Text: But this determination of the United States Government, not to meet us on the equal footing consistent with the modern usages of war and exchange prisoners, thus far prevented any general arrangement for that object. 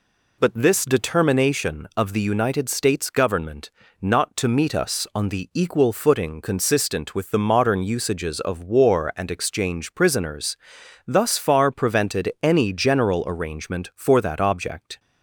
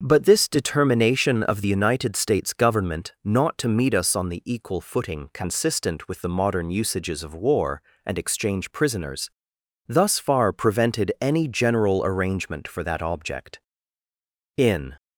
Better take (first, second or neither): first